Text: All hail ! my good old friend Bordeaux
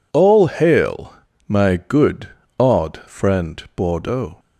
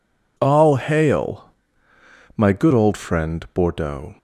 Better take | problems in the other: second | says "odd" for "old"; at 2.5 s

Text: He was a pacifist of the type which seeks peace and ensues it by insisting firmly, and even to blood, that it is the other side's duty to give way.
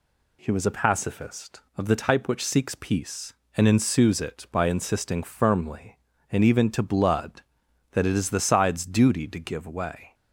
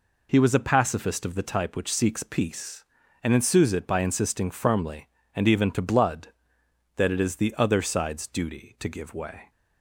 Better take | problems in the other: second | skips "other"; at 8.3 s

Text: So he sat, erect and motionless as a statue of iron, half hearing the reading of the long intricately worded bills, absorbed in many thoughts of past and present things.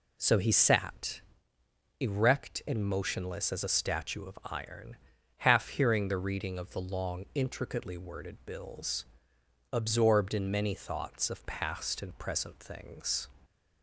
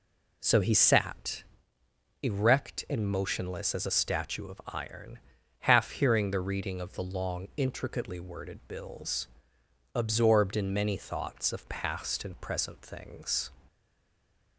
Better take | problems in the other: first | stays silent after the last word; slight; from 13.6 s on; 0.9 s long

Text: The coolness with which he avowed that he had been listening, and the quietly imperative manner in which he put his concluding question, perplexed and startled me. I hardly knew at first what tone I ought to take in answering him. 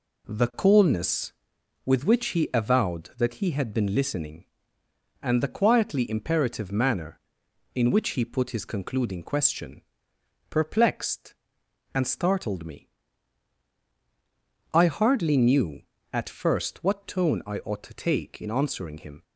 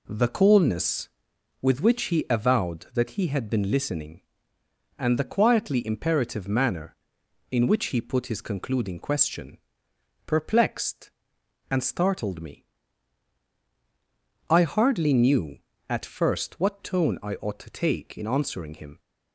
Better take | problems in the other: neither | none

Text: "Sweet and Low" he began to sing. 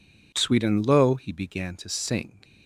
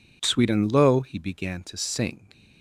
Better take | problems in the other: neither | none

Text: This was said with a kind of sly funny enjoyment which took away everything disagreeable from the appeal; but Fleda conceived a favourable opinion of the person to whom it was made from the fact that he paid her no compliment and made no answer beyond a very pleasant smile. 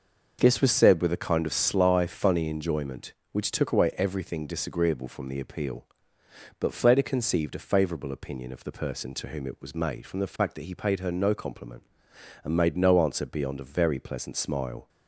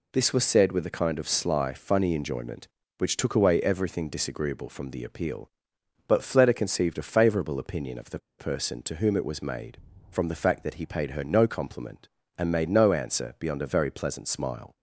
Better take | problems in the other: first | pauses between "the" and "person"; slight; at 8.1 s; 0.19 s long

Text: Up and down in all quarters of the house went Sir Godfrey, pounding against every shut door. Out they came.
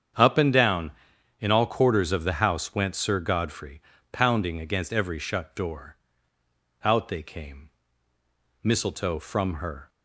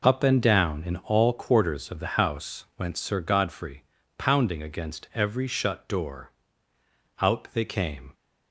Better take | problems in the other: second | starts louder than the rest; strong; until 1.6 s; 8 dB // goes on to say "Mistletoe from her"; noticeable; from 8.6 s on; 1.2 s long

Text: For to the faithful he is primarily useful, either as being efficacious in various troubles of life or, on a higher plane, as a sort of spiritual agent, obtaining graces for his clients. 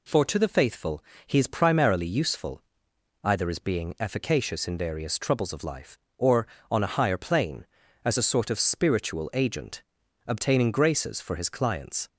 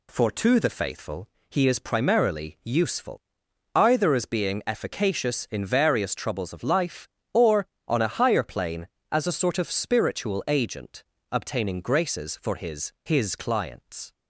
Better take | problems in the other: first | pauses between "faithful" and "he"; slight; at 1.2 s; 0.22 s long; slight in the first // says "his" twice; at 13.0 s

